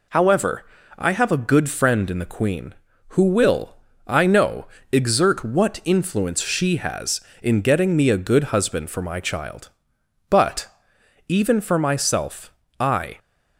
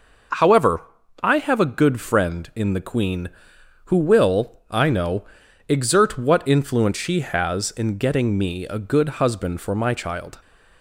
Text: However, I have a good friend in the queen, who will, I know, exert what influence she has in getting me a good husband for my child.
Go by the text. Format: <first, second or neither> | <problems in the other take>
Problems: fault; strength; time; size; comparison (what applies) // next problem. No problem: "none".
second | goes on to say "But even for myself I"; strong; from 10.3 s on; 2.8 s long